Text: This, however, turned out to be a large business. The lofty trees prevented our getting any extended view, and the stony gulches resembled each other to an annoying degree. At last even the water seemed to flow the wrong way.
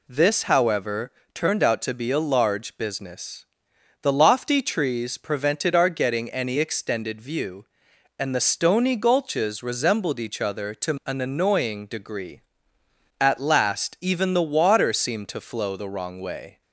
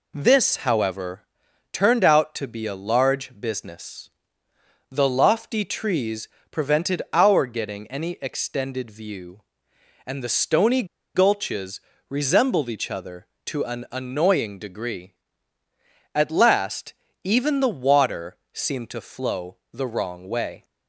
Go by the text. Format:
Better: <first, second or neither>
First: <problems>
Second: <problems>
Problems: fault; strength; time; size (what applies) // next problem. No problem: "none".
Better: first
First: none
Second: pauses between "trees" and "prevented"; slight; at 6.2 s; 0.24 s long // pauses between "stony" and "gulches"; slight; at 10.8 s; 0.30 s long // pauses between "gulches" and "resembled"; slight; at 11.7 s; 0.32 s long // pauses between "last" and "even"; slight; at 16.9 s; 0.30 s long // pauses between "water" and "seemed"; slight; at 18.3 s; 0.18 s long